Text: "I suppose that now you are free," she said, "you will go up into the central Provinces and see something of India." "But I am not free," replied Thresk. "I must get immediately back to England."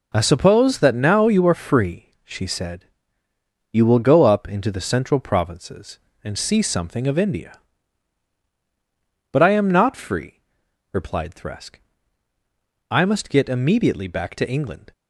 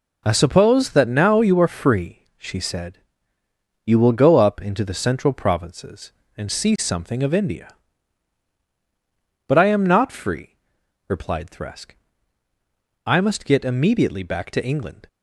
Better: neither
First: none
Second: none

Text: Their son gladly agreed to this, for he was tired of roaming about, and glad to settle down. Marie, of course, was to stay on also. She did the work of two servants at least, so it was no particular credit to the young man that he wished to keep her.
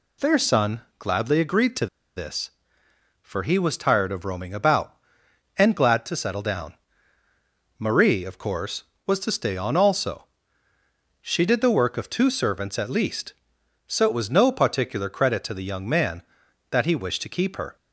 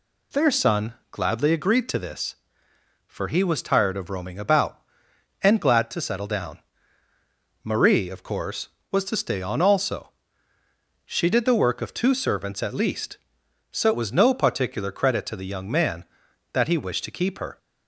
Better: second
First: pauses between "son" and "gladly"; slight; at 0.8 s; 0.18 s long // pauses between "to" and "this"; slight; at 1.8 s; 0.30 s long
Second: pauses between "son" and "gladly"; slight; at 0.9 s; 0.18 s long

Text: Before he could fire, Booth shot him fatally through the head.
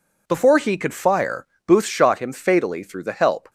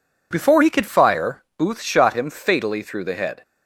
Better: second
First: says "help" for "head"; at 3.1 s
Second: none

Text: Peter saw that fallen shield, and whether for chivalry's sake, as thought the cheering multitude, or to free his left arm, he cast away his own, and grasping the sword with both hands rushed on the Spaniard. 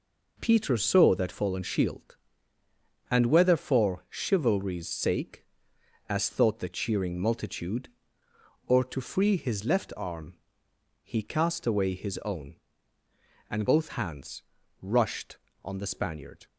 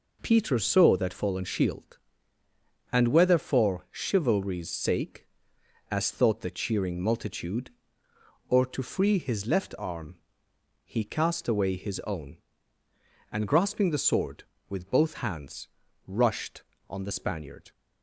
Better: second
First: skips "grasping the sword with"; at 13.6 s // pauses between "hands" and "rushed"; at 14.4 s; 0.38 s long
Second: pauses between "hands" and "rushed"; at 15.6 s; 0.38 s long

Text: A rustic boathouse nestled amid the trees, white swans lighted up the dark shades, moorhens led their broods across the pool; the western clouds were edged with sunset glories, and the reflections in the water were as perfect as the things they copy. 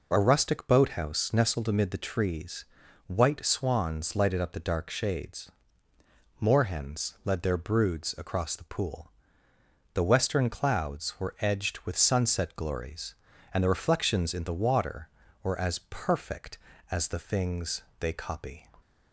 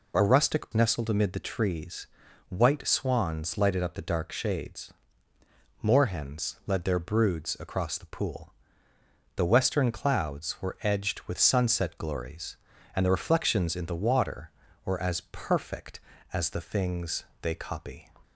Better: first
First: pauses between "things" and "they"; slight; at 17.8 s; 0.18 s long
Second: skips "boathouse"; at 0.7 s // pauses between "things" and "they"; slight; at 17.2 s; 0.18 s long

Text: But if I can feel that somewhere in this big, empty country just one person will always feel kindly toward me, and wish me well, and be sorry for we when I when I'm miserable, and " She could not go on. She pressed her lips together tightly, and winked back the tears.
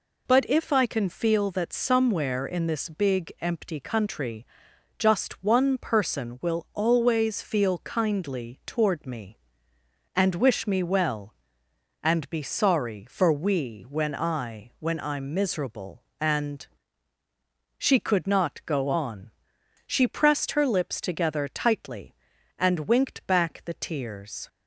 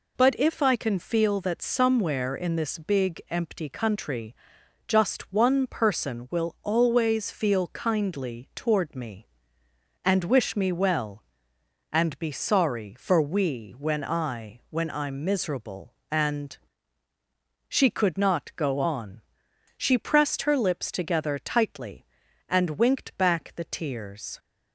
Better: neither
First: pauses between "country" and "just"; noticeable; at 4.4 s; 0.52 s long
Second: pauses between "country" and "just"; noticeable; at 4.3 s; 0.52 s long

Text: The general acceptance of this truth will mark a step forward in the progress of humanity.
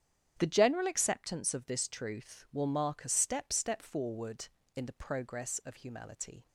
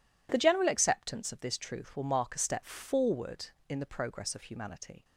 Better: second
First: starts louder than the rest; strong; until 1.4 s; 9.5 dB // says "step" twice; at 3.5 s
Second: none

